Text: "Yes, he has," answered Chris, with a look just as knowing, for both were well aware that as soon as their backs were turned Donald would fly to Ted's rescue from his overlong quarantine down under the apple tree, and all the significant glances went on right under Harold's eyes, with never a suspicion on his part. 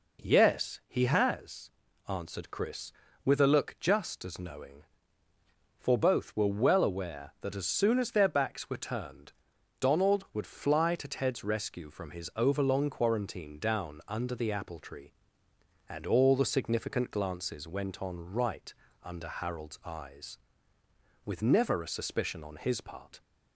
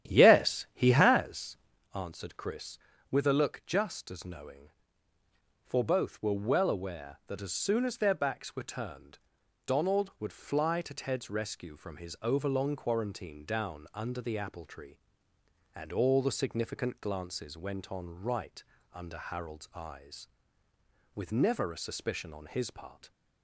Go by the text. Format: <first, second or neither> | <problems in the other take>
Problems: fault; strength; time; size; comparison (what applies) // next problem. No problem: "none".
first | starts louder than the rest; strong; until 1.9 s; 11 dB // pauses between "turned" and "Donald"; noticeable; at 9.1 s; 0.48 s long; noticeable in the first // pauses between "right" and "under"; slight; at 18.6 s; 0.30 s long; slight in the first